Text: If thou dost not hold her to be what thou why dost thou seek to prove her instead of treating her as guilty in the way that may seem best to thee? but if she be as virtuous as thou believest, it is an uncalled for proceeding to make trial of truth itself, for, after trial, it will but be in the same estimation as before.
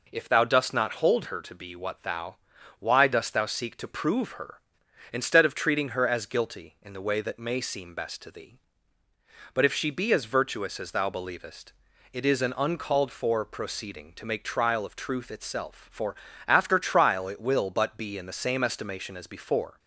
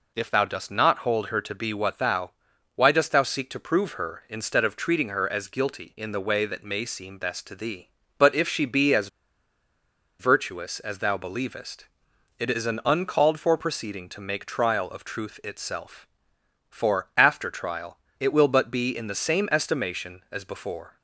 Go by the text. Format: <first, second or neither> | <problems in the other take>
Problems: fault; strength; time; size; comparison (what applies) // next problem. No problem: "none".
first | pauses between "thou" and "why"; noticeable; at 2.3 s; 0.46 s long; also in the first // pauses between "as" and "virtuous"; at 9.0 s; 1.1 s long